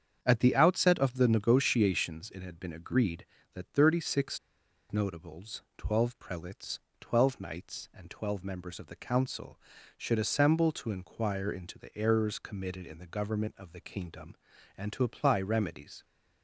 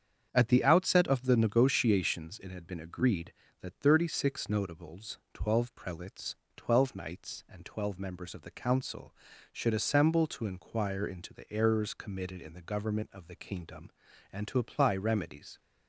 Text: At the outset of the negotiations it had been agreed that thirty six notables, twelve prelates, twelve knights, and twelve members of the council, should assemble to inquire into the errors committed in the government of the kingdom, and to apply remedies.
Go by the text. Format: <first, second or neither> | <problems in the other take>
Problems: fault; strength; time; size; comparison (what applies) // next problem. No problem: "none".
second | starts louder than the rest; strong; until 1.2 s; 7.5 dB; strong in the second // pauses between "six" and "notables"; noticeable; at 4.3 s; 0.51 s long